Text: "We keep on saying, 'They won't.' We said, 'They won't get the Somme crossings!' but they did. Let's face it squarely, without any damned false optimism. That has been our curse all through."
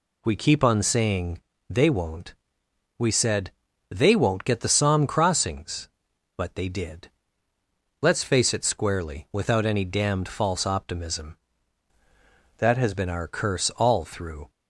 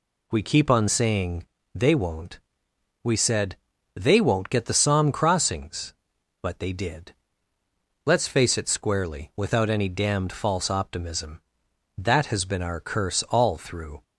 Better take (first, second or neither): second